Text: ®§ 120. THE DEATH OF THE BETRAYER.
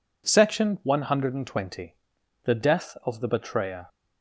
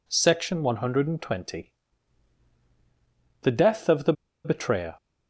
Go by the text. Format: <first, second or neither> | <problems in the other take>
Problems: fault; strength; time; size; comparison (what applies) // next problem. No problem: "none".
first | pauses between "THE" and "BETRAYER"; slight; at 4.1 s; 0.32 s long